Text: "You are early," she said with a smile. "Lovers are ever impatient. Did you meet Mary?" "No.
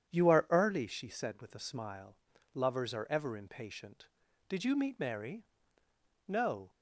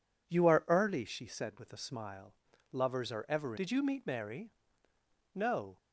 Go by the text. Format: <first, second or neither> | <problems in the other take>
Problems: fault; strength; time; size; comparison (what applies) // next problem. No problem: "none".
first | skips "impatient"; at 3.5 s